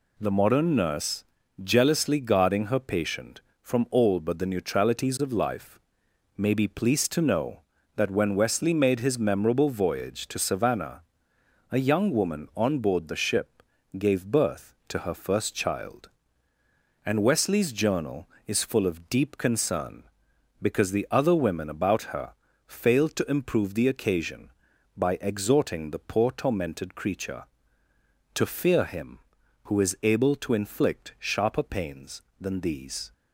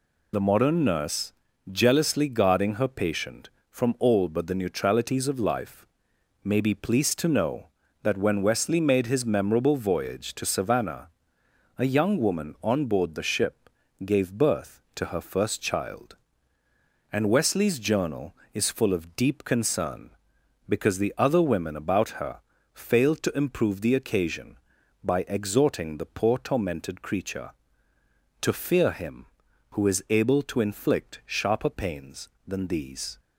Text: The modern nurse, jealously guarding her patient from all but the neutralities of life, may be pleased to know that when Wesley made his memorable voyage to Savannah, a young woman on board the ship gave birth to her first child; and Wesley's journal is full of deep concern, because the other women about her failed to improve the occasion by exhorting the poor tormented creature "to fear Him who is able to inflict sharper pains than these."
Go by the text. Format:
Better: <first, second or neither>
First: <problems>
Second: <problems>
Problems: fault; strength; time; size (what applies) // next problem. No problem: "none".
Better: first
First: pauses between "ship" and "gave"; slight; at 13.6 s; 0.34 s long // pauses between "her" and "failed"; slight; at 22.3 s; 0.34 s long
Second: loses the start of "The"; at 0.3 s; 50 ms // pauses between "ship" and "gave"; slight; at 13.6 s; 0.34 s long // pauses between "her" and "failed"; slight; at 22.3 s; 0.34 s long